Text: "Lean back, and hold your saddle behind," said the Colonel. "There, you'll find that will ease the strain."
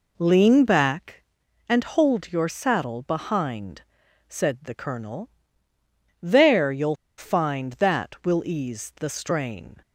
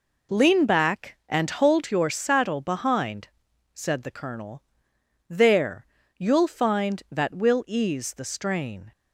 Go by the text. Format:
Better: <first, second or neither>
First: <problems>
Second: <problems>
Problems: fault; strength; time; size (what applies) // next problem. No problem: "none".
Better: second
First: pauses between "you'll" and "find"; slight; at 6.9 s; 0.22 s long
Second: none